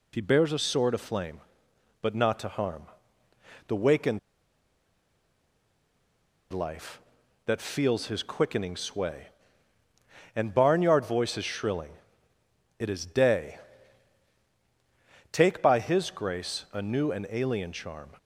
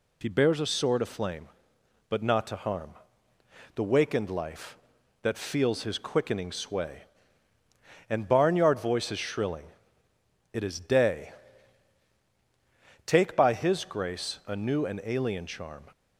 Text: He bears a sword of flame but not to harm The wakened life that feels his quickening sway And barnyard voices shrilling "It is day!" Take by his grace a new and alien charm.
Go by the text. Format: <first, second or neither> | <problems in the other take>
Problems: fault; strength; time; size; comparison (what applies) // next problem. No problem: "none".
second | pauses between "harm" and "The"; noticeable; at 2.8 s; 0.82 s long; noticeable in the second // pauses between "wakened" and "life"; strong; at 4.1 s; 2.3 s long // pauses between "shrilling" and "It"; noticeable; at 11.9 s; 0.84 s long; noticeable in the second